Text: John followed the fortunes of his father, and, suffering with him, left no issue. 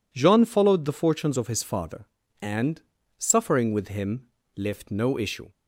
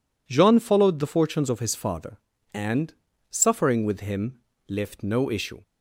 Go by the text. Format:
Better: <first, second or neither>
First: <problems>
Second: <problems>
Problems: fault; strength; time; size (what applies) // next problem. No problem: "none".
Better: neither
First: none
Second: none